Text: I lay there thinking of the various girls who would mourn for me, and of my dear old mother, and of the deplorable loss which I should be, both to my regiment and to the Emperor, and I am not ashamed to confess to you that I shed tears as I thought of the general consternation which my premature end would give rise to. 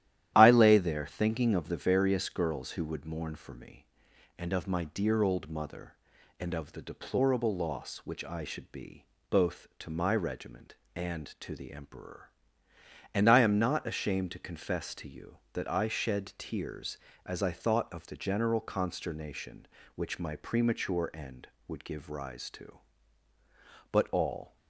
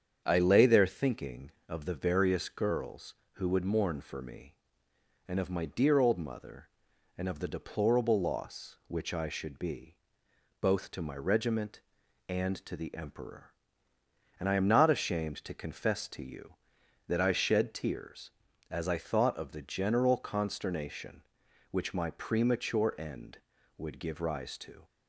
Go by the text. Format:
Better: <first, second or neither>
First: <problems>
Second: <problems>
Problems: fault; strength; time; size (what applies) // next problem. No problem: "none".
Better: second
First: starts louder than the rest; strong; until 1.3 s; 12 dB // goes on to say "But all"; noticeable; from 23.9 s on; 0.64 s long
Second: starts louder than the rest; strong; until 1.2 s; 8 dB